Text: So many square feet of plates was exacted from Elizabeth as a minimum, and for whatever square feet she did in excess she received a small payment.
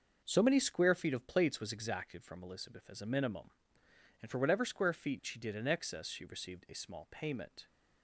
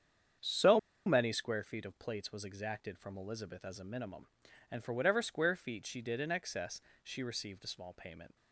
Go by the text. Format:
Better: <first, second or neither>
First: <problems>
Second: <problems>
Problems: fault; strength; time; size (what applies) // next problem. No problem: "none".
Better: first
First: none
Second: starts louder than the rest; strong; until 1.6 s; 8 dB // pauses between "So" and "many"; slight; at 0.7 s; 0.27 s long // pauses between "excess" and "she"; slight; at 6.8 s; 0.22 s long